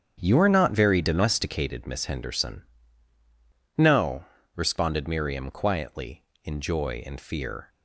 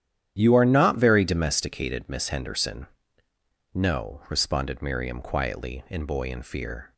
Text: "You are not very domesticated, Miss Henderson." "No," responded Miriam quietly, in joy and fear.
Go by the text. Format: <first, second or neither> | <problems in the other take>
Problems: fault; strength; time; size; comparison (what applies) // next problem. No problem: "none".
first | starts louder than the rest; strong; until 1.4 s; 10 dB; strong in the first // says "boy" for "joy"; at 6.0 s